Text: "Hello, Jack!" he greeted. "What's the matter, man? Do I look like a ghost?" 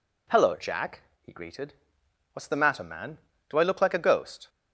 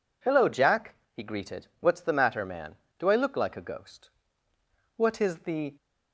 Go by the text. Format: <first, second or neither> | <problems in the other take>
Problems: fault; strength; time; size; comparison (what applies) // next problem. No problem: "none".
first | goes on to say "What is the"; noticeable; from 4.9 s on; 0.78 s long